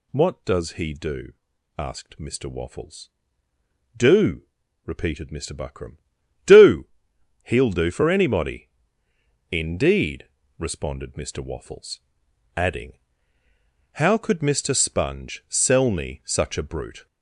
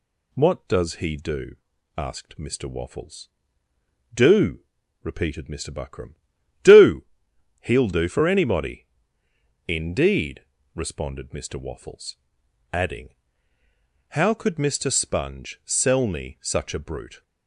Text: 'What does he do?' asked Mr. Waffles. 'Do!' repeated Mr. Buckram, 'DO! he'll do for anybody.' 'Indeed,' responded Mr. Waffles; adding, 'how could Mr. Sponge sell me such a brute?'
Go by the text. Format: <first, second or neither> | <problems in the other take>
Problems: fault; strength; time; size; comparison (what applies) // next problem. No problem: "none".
second | gets louder; noticeable; throughout; 4.5 dB